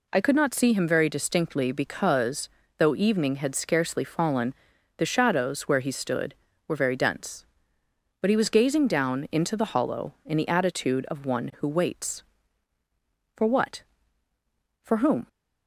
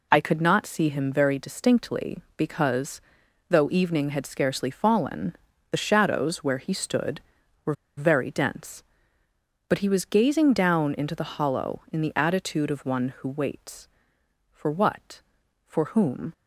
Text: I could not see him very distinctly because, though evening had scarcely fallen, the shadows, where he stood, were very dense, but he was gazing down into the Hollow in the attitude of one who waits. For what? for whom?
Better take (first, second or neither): first